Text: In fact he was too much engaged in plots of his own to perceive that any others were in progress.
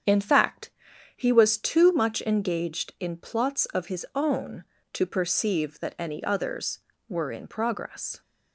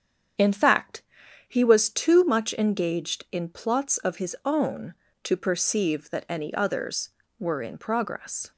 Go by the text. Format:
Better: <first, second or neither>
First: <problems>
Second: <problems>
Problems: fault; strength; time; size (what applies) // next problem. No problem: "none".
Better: neither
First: starts louder than the rest; strong; until 1.5 s; 8 dB // pauses between "fact" and "he"; at 0.7 s; 0.44 s long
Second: starts louder than the rest; strong; until 1.8 s; 8 dB // pauses between "fact" and "he"; at 1.0 s; 0.44 s long